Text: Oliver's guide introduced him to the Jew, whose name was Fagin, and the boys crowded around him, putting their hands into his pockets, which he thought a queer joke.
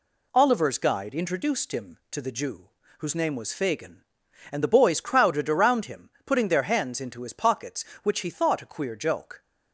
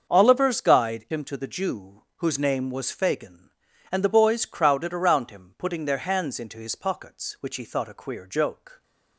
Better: first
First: none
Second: starts louder than the rest; until 1.1 s; 6.5 dB // skips "introduced"; at 1.0 s

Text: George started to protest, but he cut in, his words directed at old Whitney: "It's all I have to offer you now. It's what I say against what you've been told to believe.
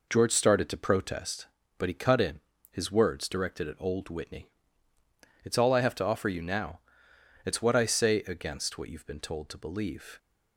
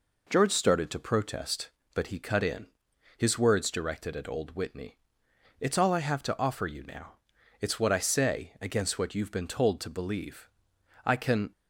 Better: first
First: none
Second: goes on to say "I can"; slight; from 11.0 s on; 0.46 s long

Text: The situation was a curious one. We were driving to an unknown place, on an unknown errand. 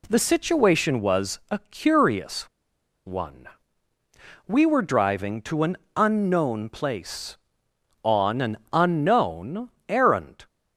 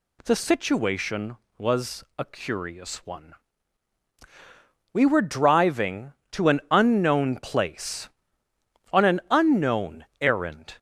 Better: second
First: pauses between "curious" and "one"; noticeable; at 2.4 s; 0.59 s long // pauses between "an" and "unknown"; slight; at 5.7 s; 0.20 s long // pauses between "unknown" and "errand"; slight; at 9.7 s; 0.18 s long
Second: none

